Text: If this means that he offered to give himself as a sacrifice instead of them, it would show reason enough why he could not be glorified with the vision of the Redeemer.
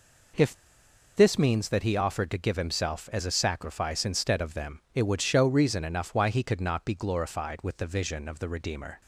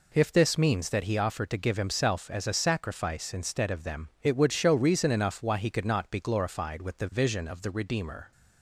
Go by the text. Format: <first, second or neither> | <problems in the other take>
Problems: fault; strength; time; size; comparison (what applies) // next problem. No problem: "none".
second | pauses between "If" and "this"; noticeable; at 0.5 s; 0.64 s long